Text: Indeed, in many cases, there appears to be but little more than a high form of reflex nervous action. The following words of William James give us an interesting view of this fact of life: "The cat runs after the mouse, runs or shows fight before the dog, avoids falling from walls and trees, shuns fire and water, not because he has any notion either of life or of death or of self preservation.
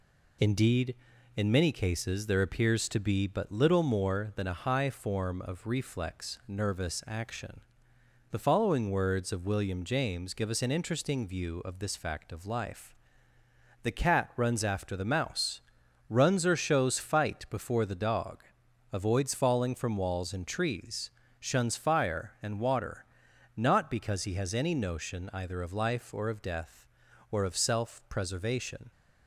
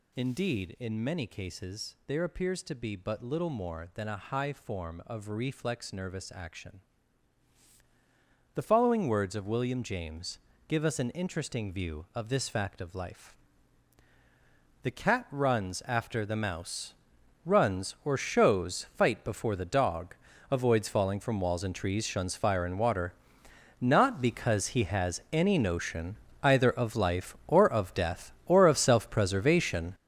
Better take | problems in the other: first | gets louder; strong; throughout; 10 dB // pauses between "James" and "give"; slight; at 10.3 s; 0.32 s long // pauses between "notion" and "either"; slight; at 26.1 s; 0.26 s long

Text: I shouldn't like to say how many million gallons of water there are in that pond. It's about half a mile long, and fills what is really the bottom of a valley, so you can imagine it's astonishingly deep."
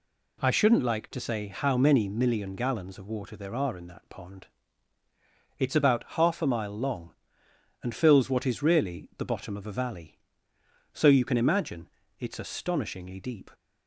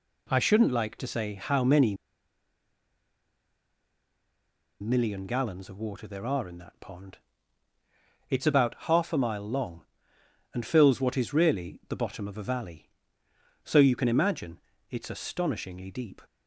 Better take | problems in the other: first | pauses between "many" and "million"; strong; at 1.9 s; 2.8 s long // pauses between "imagine" and "it's"; slight; at 14.5 s; 0.30 s long; slight in the first

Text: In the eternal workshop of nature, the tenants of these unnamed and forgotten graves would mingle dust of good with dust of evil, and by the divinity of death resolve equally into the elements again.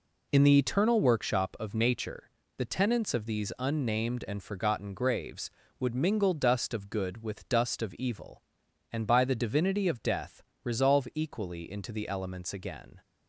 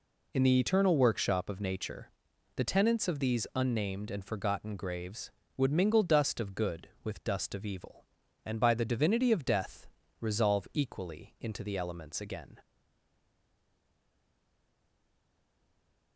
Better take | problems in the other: first | pauses between "death" and "resolve"; slight; at 9.8 s; 0.34 s long; slight in the first // stays silent after the last word; strong; from 12.6 s on; 3.5 s long

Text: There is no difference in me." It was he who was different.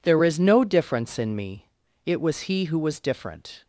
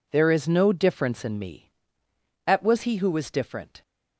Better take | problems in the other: first | says "At" for "It"; at 2.4 s

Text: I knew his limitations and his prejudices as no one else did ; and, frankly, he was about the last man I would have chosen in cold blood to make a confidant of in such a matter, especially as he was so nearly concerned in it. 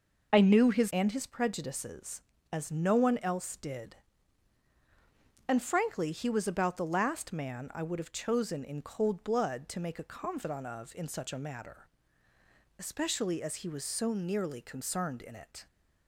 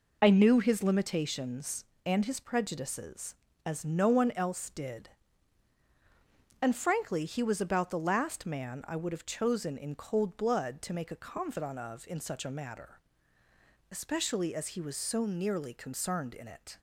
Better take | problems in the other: second | skips "limitations"; at 0.9 s

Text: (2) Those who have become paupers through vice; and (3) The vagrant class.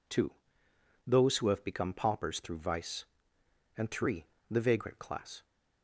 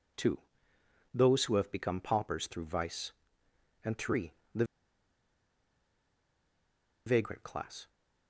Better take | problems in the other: first | pauses between "The" and "vagrant"; strong; at 4.6 s; 2.4 s long

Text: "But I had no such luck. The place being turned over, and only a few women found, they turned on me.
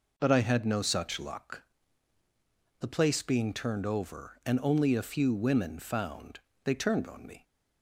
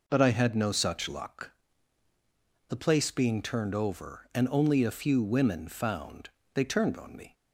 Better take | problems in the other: neither | none

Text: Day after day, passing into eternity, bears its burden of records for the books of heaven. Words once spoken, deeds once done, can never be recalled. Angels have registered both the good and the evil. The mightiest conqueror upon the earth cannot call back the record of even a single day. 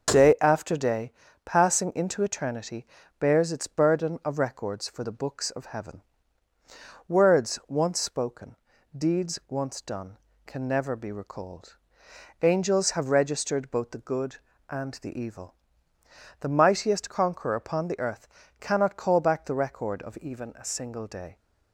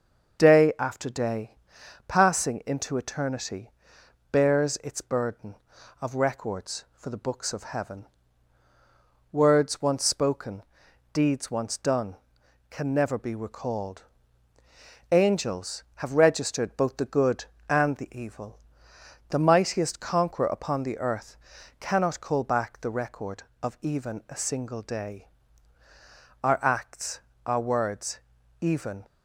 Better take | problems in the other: first | starts louder than the rest; until 1.4 s; 7 dB; also in the first // pauses between "earth" and "cannot"; at 21.3 s; 0.44 s long; slight in the first // goes on to say "Our acts our words even"; strong; from 26.4 s on; 2.6 s long

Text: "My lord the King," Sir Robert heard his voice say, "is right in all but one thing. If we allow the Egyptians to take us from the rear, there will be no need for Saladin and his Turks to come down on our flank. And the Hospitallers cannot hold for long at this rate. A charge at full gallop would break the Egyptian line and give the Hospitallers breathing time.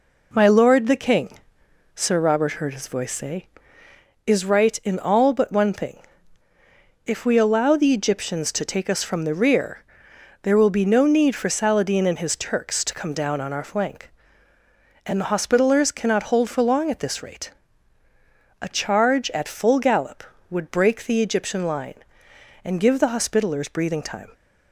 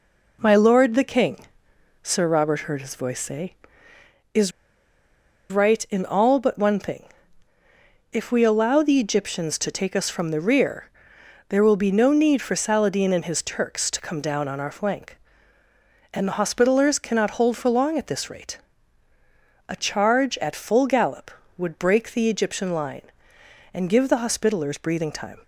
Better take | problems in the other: first | pauses between "is" and "right"; at 4.5 s; 1.0 s long

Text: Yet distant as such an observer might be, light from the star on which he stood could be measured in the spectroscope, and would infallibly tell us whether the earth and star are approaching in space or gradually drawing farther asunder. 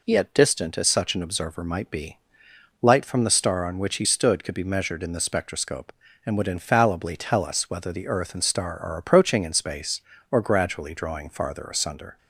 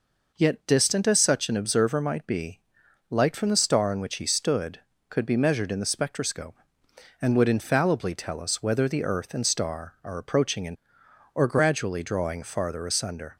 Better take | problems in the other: first | skips "space"; at 11.0 s

